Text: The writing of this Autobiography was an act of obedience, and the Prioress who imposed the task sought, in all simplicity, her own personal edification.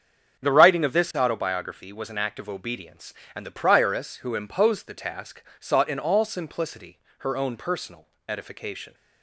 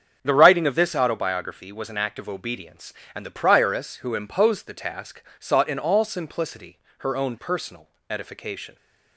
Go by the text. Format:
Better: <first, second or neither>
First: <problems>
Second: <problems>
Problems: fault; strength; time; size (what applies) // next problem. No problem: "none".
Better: neither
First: starts louder than the rest; strong; until 1.4 s; 7 dB // pauses between "task" and "sought"; slight; at 5.4 s; 0.16 s long // pauses between "personal" and "edification"; slight; at 8.0 s; 0.20 s long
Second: starts louder than the rest; strong; until 1.2 s; 7 dB // pauses between "task" and "sought"; slight; at 5.2 s; 0.16 s long // pauses between "personal" and "edification"; slight; at 7.8 s; 0.20 s long